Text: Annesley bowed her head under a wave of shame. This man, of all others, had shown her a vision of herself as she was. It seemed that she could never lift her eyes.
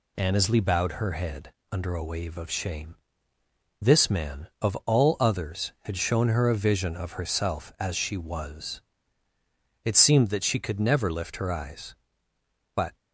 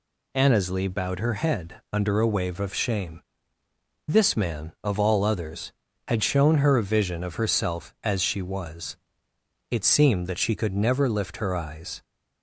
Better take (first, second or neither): second